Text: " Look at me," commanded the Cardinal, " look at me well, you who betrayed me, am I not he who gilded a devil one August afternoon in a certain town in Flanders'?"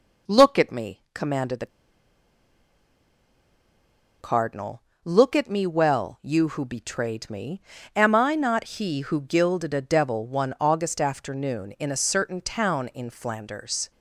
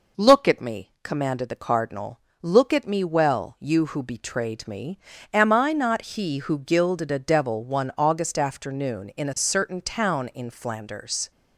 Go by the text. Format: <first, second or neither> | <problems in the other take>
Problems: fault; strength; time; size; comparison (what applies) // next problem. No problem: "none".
second | pauses between "the" and "Cardinal"; strong; at 1.6 s; 2.5 s long